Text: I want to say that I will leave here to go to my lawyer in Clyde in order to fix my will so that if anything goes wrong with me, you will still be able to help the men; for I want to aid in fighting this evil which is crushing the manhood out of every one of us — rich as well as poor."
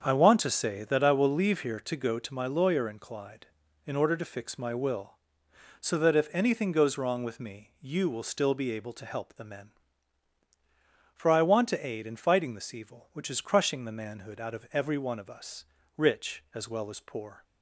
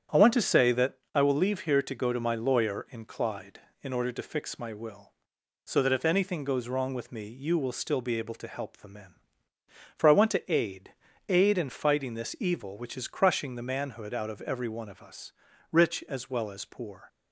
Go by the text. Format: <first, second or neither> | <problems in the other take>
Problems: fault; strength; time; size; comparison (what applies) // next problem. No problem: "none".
first | starts louder than the rest; strong; until 1.3 s; 9 dB; strong in the first // pauses between "that" and "I"; slight; at 0.9 s; 0.20 s long // says "aid" twice; at 11.2 s